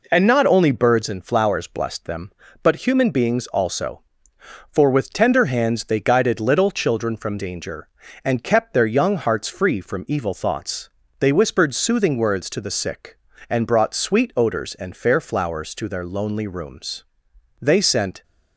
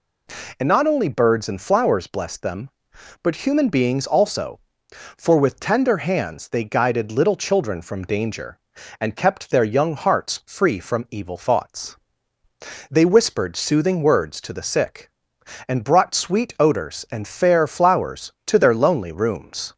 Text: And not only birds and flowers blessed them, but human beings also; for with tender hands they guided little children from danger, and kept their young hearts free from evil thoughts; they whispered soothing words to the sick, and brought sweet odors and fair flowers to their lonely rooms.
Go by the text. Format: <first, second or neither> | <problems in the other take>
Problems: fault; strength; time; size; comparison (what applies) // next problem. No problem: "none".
second | goes on to say "They sent"; noticeable; from 17.6 s on; 0.62 s long